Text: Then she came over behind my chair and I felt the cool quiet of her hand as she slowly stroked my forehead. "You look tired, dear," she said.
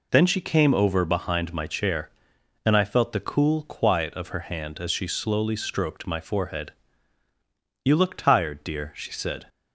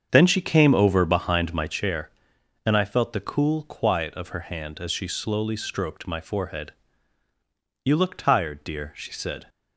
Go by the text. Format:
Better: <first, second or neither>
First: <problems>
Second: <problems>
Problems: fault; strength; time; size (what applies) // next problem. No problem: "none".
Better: first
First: none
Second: starts louder than the rest; strong; until 1.8 s; 7.5 dB